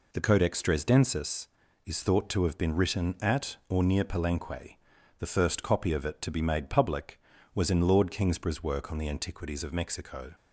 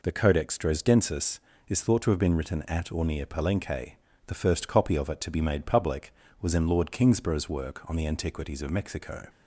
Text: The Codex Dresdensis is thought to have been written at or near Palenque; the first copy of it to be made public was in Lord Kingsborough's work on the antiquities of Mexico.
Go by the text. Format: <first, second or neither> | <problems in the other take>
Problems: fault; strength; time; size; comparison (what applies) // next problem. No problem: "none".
neither | none